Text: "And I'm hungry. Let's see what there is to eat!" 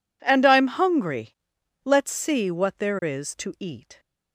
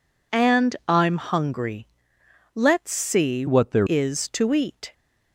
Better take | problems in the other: first | changes voice from "what" to "there"; from 3.4 to 3.8 s; 0.4 s long

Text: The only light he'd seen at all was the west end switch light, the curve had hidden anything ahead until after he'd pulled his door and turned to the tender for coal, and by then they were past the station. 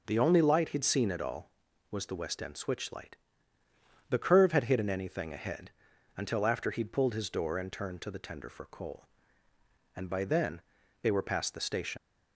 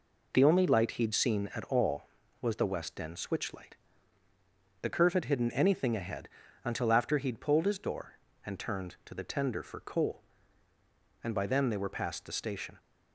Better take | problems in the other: second | pauses between "ahead" and "until"; at 5.7 s; 0.44 s long; slight in the second // pauses between "then" and "they"; at 10.6 s; 0.40 s long // leaves "station" unfinished; at 11.9 s; 70 ms

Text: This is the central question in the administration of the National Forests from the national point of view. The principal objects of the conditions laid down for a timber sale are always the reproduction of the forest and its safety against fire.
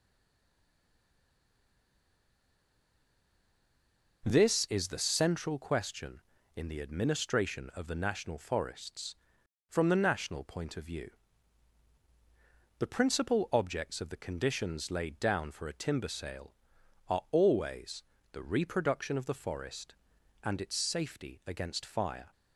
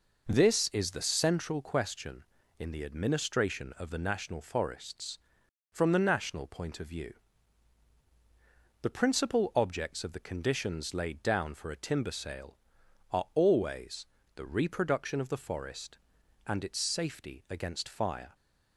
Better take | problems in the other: second | stays silent before the first word; strong; until 4.2 s; 4.2 s long // pauses between "always" and "the"; slight; at 18.0 s; 0.28 s long; slight in the second

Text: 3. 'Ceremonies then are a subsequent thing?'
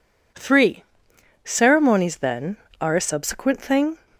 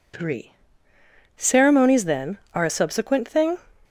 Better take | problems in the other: neither | none

